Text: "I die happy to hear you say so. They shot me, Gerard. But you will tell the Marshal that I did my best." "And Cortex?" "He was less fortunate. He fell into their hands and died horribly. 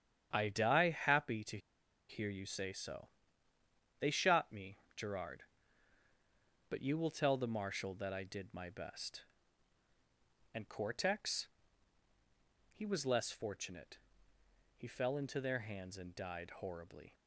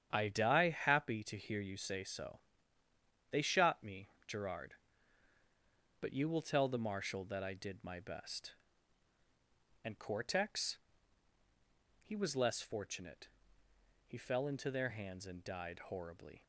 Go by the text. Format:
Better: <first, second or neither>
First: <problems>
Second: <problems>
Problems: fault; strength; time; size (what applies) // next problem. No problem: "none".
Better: second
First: starts louder than the rest; strong; until 1.3 s; 8.5 dB // pauses between "to" and "hear"; noticeable; at 1.5 s; 0.51 s long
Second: starts louder than the rest; strong; until 1.1 s; 8.5 dB